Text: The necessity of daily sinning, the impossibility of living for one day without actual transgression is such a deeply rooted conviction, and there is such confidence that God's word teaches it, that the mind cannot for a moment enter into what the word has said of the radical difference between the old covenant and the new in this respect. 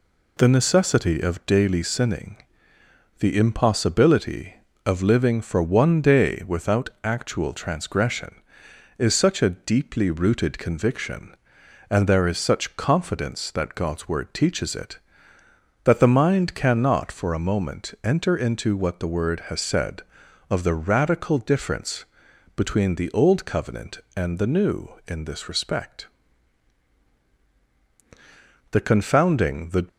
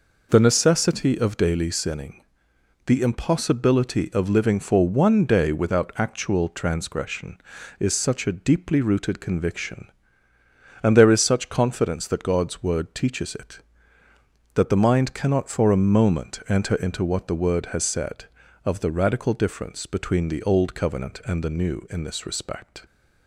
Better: second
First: pauses between "difference" and "between"; noticeable; at 22.0 s; 0.52 s long // goes on to say "The confounding the"; noticeable; from 28.7 s on; 1.1 s long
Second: none

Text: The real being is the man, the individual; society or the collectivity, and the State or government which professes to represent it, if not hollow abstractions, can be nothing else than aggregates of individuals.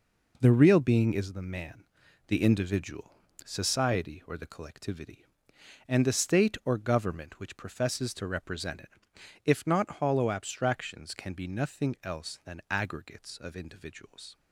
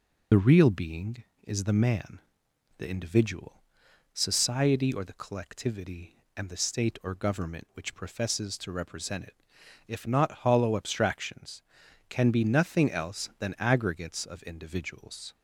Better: first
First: none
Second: loses the start of "The"; at 0.3 s; 55 ms

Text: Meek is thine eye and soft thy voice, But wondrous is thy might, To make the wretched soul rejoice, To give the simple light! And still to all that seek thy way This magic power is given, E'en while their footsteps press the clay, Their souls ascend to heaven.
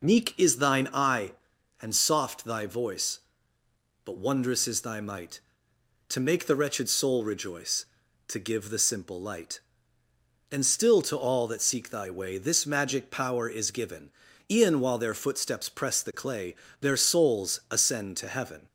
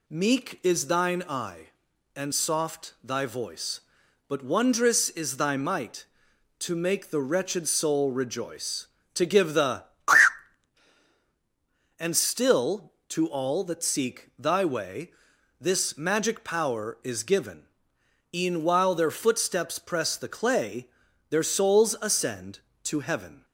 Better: first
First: none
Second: skips "simple light"; at 10.9 s // pauses between "way" and "This"; noticeable; at 15.0 s; 0.50 s long

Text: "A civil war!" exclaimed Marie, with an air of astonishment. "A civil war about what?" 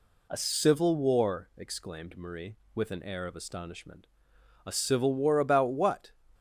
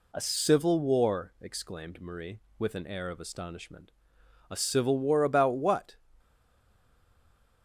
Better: first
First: none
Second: stays silent after the last word; noticeable; from 6.1 s on; 1.5 s long

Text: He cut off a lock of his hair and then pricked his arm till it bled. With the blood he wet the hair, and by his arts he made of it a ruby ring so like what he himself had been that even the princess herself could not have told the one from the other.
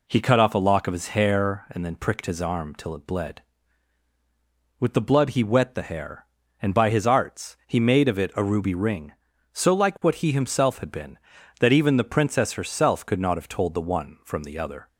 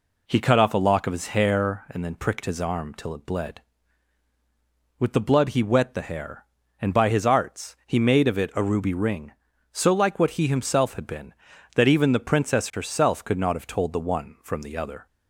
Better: neither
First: none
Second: none

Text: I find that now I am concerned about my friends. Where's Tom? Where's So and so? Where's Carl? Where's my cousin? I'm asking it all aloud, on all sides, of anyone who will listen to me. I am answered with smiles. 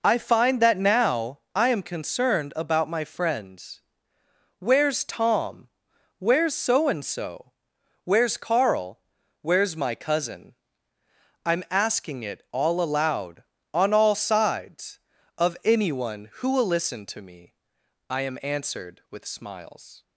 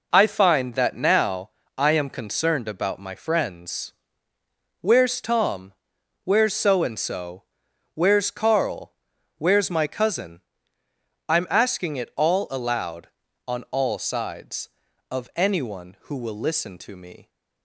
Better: first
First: none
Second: pauses between "now" and "I"; slight; at 1.5 s; 0.26 s long // stops before "I am answered with smiles"; at 17.2 s

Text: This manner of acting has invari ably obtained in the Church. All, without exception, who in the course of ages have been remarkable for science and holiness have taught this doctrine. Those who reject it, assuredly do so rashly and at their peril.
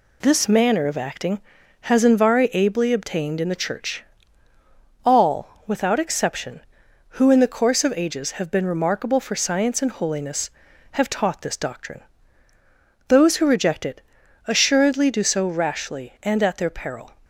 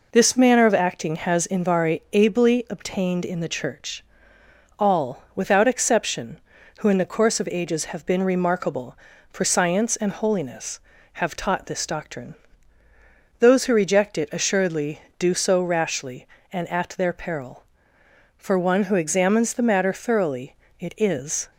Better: first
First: none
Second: goes on to say "For one who examines the matter thoroughly it is"; strong; from 18.3 s on; 3.1 s long

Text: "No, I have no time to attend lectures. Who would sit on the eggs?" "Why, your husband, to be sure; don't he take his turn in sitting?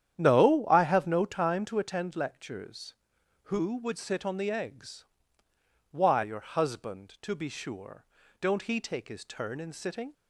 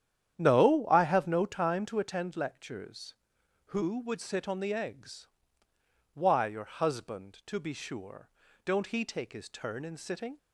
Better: neither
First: starts louder than the rest; strong; until 1.2 s; 10 dB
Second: starts louder than the rest; strong; until 1.4 s; 10 dB

